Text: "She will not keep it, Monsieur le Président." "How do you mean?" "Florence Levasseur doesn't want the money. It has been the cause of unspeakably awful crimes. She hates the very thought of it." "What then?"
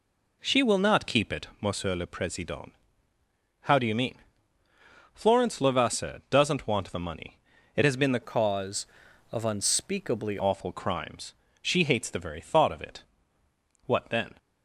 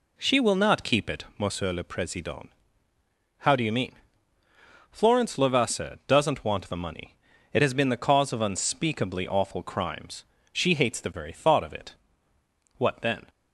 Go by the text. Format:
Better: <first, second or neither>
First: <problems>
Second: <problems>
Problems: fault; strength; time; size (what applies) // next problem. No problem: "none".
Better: second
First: changes voice from "cause" to "unspeakably"; from 8.2 to 10.3 s; 2.1 s long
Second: none